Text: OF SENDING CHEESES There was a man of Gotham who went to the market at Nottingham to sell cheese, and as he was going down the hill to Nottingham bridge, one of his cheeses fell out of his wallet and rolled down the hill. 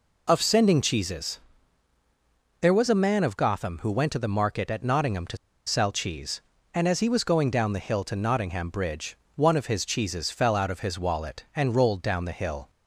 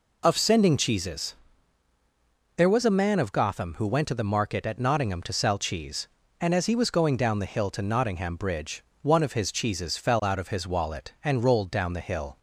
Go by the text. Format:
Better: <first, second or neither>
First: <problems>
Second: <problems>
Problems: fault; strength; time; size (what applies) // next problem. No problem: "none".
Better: second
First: pauses between "CHEESES" and "There"; at 1.3 s; 1.2 s long // pauses between "to" and "sell"; slight; at 5.3 s; 0.30 s long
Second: pauses between "CHEESES" and "There"; at 1.3 s; 1.2 s long